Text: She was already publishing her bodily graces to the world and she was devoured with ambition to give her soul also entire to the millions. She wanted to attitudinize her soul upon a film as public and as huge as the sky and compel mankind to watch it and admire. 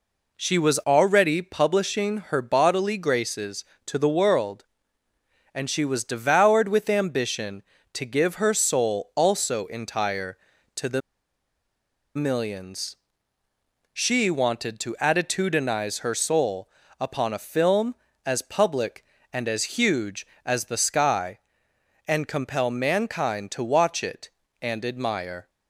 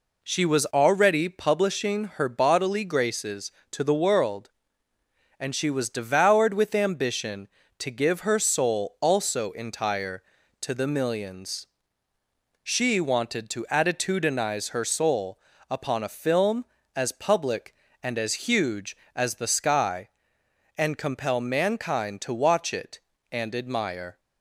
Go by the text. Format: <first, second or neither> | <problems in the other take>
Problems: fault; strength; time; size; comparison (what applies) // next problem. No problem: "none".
second | pauses between "the" and "millions"; at 11.0 s; 1.1 s long // pauses between "soul" and "upon"; slight; at 16.6 s; 0.30 s long; slight in the second